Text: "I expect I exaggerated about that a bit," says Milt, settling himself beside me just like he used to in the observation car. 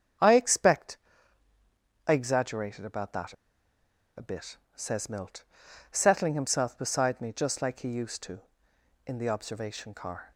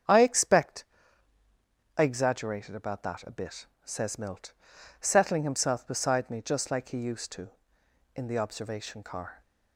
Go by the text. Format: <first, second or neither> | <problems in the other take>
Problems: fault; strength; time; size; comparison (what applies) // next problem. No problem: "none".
second | starts louder than the rest; strong; until 2.3 s; 7.5 dB; strong in the second // pauses between "expect" and "I"; at 0.9 s; 1.1 s long; also in the second // pauses between "that" and "a"; noticeable; at 3.3 s; 0.83 s long